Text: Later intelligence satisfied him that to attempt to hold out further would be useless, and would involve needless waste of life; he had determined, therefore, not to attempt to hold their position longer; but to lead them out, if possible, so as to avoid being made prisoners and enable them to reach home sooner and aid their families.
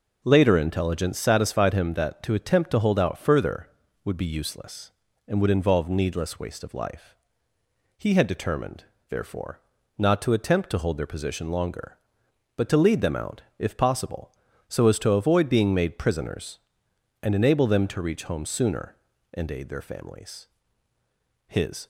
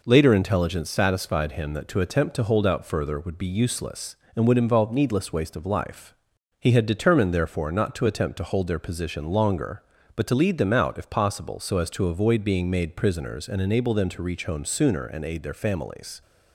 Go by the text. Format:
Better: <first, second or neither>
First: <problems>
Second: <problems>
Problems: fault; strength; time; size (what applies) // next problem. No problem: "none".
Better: second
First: goes on to say "His"; slight; from 21.4 s on; 0.40 s long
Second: none